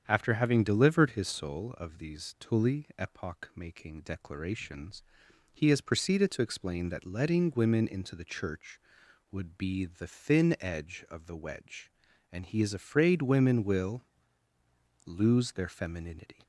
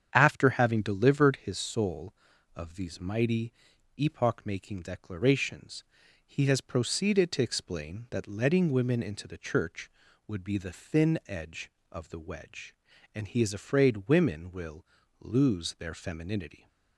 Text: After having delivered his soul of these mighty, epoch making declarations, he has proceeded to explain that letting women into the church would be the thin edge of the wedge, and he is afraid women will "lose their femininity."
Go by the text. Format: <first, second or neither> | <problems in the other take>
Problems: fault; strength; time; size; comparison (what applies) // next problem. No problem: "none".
second | starts louder than the rest; strong; until 1.0 s; 8 dB; strong in the second // says "tully" for "mighty"; at 2.3 s // pauses between "will" and "lose"; at 14.0 s; 1.0 s long; slight in the second